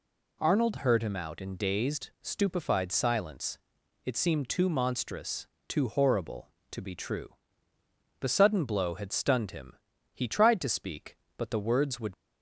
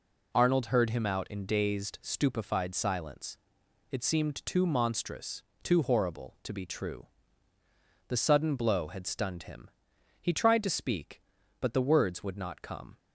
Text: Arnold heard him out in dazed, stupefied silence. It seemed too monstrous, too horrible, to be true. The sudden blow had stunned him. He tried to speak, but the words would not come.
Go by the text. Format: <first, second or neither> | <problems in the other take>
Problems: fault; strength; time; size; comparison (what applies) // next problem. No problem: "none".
second | stops before "not come"; at 12.1 s